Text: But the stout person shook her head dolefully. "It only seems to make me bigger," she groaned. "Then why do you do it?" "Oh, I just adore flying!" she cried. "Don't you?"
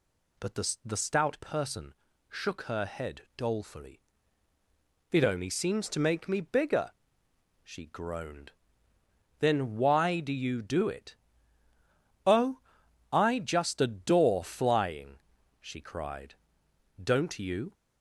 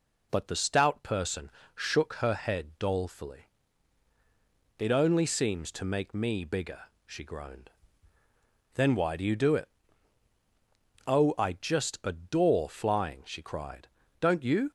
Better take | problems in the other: second | says "the" twice; at 0.8 s // pauses between "person" and "shook"; slight; at 1.9 s; 0.36 s long; slight in the second // pauses between "head" and "dolefully"; slight; at 3.2 s; 0.16 s long

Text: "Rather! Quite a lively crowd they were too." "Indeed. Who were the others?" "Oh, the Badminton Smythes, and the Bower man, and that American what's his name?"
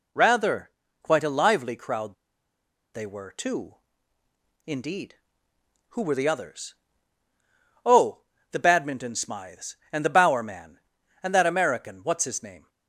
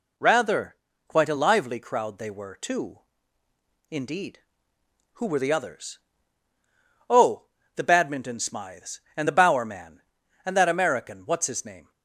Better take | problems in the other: second | pauses between "crowd" and "they"; noticeable; at 2.1 s; 0.79 s long

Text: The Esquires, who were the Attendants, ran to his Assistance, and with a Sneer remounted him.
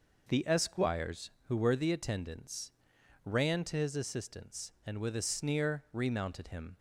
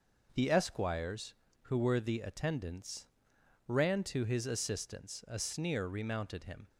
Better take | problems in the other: first | skips "and with"; at 5.2 s

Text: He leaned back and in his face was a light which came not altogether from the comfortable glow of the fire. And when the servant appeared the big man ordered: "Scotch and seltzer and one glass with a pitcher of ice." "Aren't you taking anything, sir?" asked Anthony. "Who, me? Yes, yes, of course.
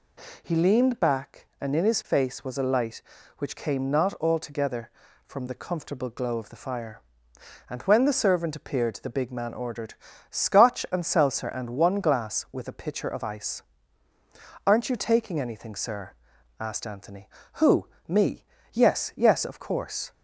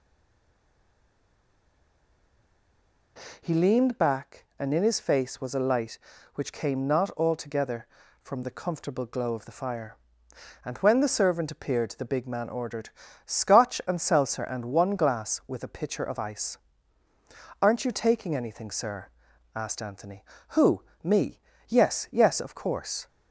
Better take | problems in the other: first | stays silent before the first word; strong; until 3.1 s; 3.1 s long

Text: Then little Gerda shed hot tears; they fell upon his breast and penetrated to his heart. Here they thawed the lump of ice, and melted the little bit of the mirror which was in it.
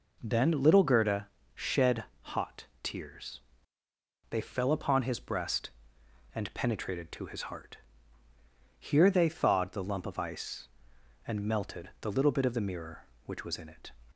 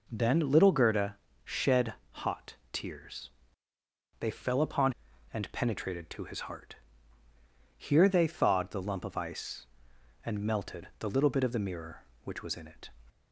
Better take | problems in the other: first | pauses between "Gerda" and "shed"; slight; at 1.1 s; 0.28 s long; slight in the first // pauses between "shed" and "hot"; slight; at 1.9 s; 0.20 s long; slight in the first // pauses between "hot" and "tears"; slight; at 2.5 s; 0.16 s long; slight in the first // skips "his breast"; at 5.1 s

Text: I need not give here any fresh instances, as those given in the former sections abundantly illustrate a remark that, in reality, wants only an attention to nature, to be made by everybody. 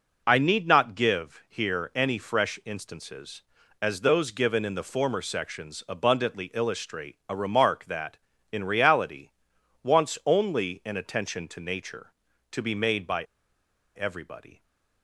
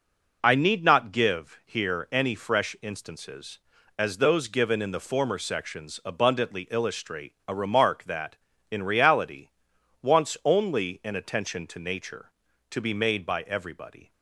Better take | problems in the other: second | pauses between "by" and "everybody"; noticeable; at 13.2 s; 0.72 s long

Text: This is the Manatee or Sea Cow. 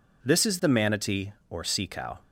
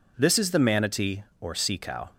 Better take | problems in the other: neither | none

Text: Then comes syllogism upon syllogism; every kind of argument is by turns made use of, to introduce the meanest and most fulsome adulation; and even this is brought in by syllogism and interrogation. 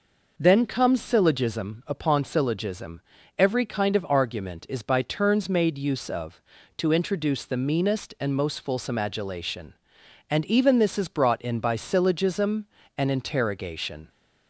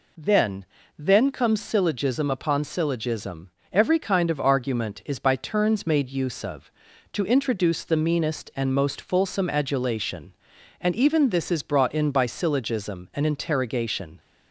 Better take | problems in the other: first | says "Then" twice; at 0.9 s

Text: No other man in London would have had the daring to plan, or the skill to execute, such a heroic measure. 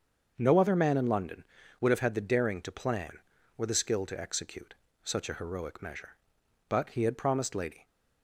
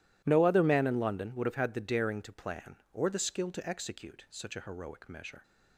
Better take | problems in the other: second | starts louder than the rest; until 1.3 s; 6.5 dB // goes on to say "But he had promised Lady"; noticeable; from 6.6 s on; 1.1 s long

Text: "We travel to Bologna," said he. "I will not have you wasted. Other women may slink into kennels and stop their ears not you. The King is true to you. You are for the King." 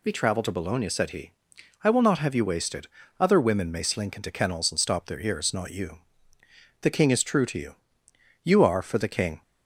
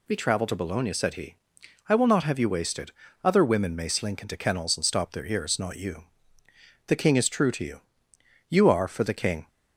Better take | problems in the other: neither | none

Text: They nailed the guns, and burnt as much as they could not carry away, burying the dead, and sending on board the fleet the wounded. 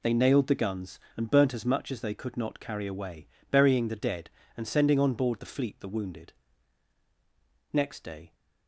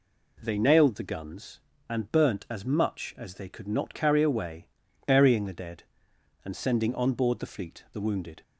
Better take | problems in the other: second | goes on to say "Next day"; noticeable; from 7.7 s on; 0.62 s long

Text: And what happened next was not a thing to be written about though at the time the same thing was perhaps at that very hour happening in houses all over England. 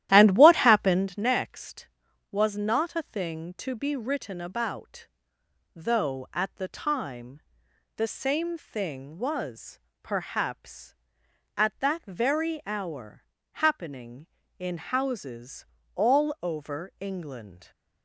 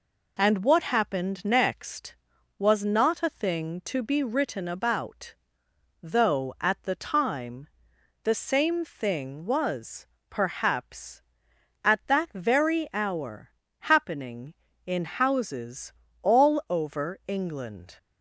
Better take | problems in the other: second | starts louder than the rest; strong; until 1.2 s; 13 dB // pauses between "about" and "though"; noticeable; at 5.0 s; 0.66 s long; noticeable in the second // pauses between "time" and "the"; noticeable; at 7.4 s; 0.54 s long; noticeable in the second // pauses between "was" and "perhaps"; slight; at 9.7 s; 0.24 s long; slight in the second // pauses between "hour" and "happening"; slight; at 13.2 s; 0.30 s long; slight in the second // pauses between "houses" and "all"; slight; at 15.6 s; 0.30 s long; slight in the second

